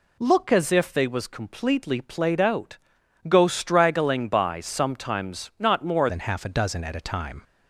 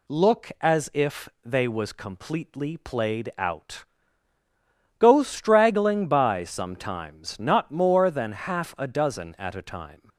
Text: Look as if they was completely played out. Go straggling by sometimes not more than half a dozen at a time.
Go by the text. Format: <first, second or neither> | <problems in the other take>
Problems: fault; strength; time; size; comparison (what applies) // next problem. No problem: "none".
second | changes voice at "than"; from 6.0 s on; 1.4 s long